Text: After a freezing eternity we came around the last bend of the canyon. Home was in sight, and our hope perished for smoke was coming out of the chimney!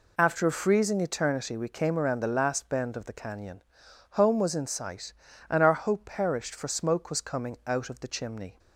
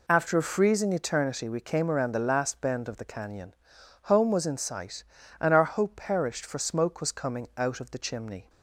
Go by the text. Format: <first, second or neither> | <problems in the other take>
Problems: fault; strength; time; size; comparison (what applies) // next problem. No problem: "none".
neither | none